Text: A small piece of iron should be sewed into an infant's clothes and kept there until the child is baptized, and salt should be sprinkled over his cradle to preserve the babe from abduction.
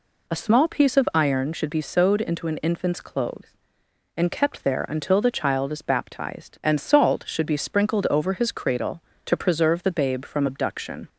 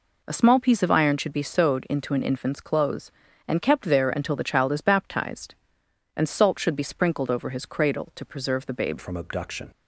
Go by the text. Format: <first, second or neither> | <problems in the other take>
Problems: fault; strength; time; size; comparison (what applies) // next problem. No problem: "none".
first | changes voice at "from"; from 8.9 s on; 0.8 s long